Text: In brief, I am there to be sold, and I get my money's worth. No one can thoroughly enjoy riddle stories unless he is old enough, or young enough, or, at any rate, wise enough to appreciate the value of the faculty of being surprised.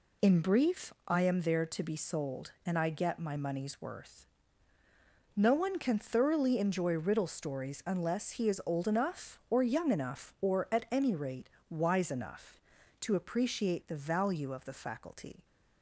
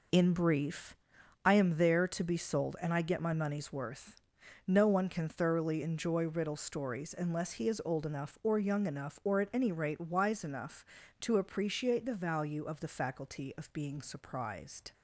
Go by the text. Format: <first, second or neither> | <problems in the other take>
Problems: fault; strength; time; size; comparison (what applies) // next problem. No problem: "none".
second | stops before "of being surprised"; at 15.4 s